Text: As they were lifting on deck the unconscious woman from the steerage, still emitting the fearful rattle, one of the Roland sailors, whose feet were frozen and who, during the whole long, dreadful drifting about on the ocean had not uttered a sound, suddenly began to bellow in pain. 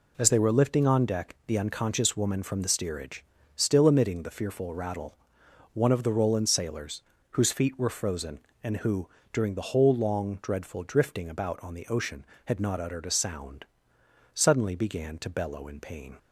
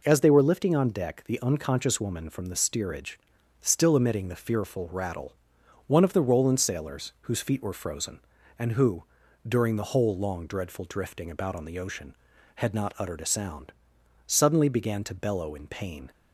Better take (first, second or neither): neither